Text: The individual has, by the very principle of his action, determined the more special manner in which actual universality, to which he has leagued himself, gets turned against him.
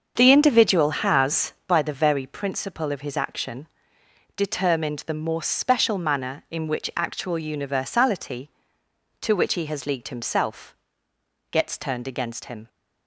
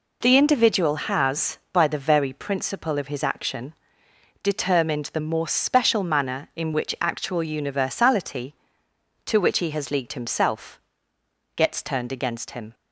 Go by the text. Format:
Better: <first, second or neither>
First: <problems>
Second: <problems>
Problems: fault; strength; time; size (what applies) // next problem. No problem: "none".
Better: second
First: starts louder than the rest; until 1.7 s; 7 dB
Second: none